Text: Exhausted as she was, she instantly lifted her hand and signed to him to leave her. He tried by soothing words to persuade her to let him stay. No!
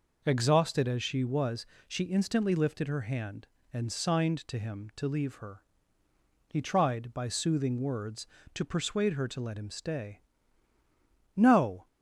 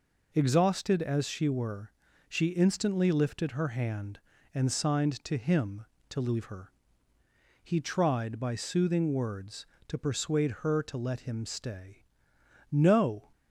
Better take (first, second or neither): first